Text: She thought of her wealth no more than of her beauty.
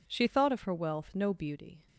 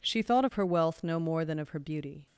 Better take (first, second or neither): second